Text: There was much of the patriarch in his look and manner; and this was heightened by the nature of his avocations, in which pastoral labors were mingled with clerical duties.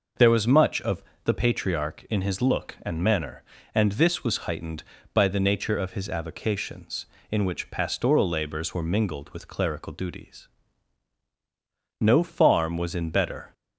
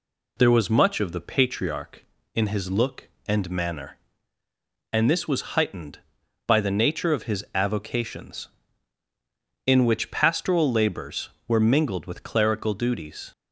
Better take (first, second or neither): second